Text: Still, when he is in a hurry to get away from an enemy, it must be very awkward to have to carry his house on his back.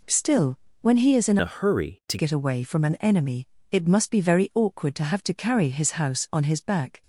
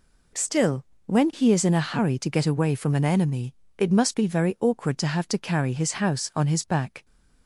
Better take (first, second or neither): second